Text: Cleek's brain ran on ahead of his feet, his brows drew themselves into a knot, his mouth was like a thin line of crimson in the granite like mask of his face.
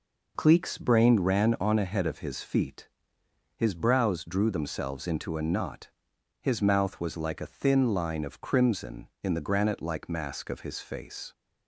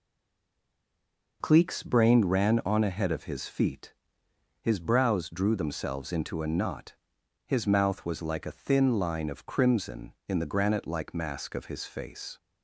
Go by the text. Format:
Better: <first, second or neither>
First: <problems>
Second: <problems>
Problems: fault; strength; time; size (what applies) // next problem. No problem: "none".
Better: first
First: none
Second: stays silent before the first word; noticeable; until 1.4 s; 1.4 s long